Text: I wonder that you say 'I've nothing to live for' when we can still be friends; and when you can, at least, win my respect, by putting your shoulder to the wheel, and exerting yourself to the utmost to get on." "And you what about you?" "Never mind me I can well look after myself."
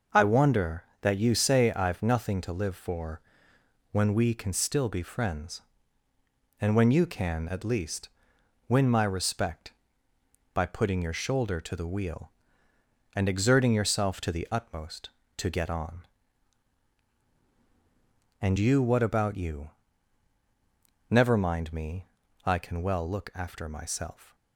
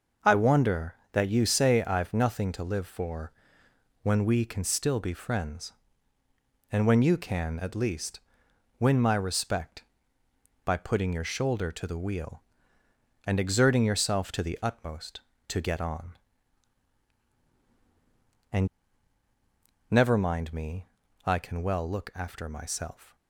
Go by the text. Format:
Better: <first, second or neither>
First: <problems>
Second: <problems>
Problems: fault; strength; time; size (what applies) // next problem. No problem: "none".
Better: first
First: pauses between "for" and "when"; noticeable; at 3.2 s; 0.70 s long // pauses between "me" and "I"; at 22.0 s; 0.38 s long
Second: pauses between "for" and "when"; noticeable; at 3.3 s; 0.70 s long // skips "you what about you"; at 19.2 s // pauses between "me" and "I"; at 20.8 s; 0.38 s long